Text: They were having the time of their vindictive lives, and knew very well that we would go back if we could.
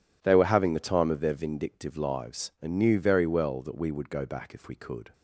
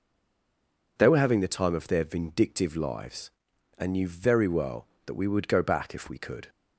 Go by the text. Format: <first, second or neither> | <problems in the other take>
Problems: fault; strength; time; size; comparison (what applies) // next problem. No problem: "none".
first | stays silent before the first word; until 0.9 s; 0.9 s long